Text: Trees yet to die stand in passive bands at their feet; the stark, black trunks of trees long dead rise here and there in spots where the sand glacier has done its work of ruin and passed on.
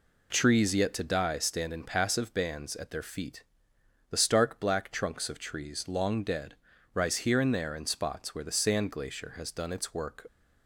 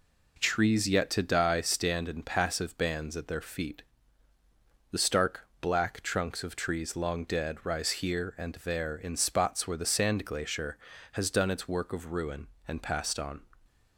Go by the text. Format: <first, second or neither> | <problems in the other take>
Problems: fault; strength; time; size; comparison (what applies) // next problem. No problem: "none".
second | pauses between "dead" and "rise"; at 6.5 s; 0.38 s long // stops before "of ruin and passed on"; at 10.2 s